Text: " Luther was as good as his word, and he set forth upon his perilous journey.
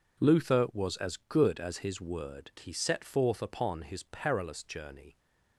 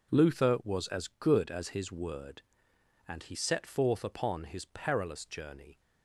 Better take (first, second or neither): second